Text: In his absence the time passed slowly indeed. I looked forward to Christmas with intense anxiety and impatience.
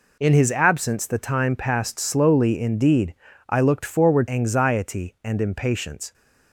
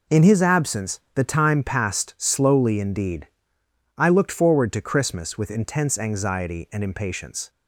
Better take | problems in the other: second | skips "to Christmas with intense"; at 4.2 s

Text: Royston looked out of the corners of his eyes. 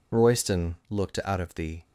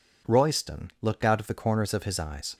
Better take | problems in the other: second | pauses between "Royston" and "looked"; slight; at 0.7 s; 0.16 s long // stops before "corners of his eyes"; at 1.8 s

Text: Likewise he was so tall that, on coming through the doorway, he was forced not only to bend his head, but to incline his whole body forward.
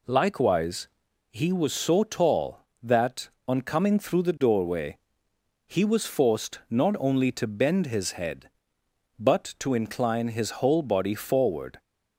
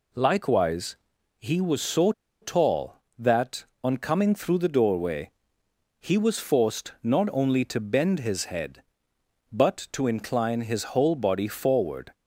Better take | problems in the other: first | pauses between "Likewise" and "he"; at 0.9 s; 0.42 s long; also in the first // pauses between "so" and "tall"; slight; at 2.1 s; 0.29 s long

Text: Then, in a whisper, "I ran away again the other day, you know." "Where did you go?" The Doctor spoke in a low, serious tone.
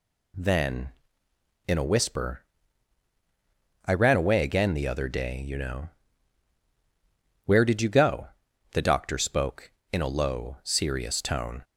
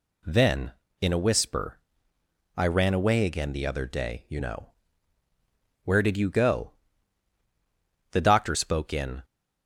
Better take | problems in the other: first | stops before "a low serious tone"; at 9.2 s

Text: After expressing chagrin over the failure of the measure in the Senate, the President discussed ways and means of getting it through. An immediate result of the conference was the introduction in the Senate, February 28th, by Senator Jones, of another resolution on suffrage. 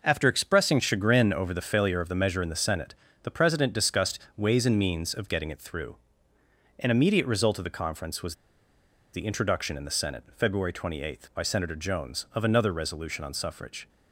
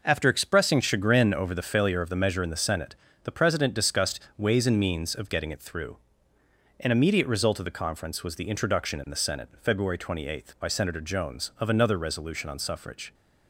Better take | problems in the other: second | pauses between "discussed" and "ways"; slight; at 4.1 s; 0.18 s long; slight in the second // pauses between "was" and "the"; noticeable; at 8.3 s; 0.78 s long

